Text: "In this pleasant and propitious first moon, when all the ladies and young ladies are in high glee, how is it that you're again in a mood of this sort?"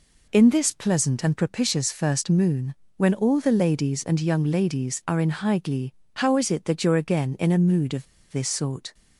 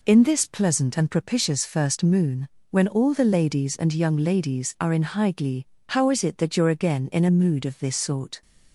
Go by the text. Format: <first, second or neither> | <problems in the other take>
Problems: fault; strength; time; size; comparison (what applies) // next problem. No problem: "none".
second | pauses between "of" and "this"; slight; at 8.0 s; 0.26 s long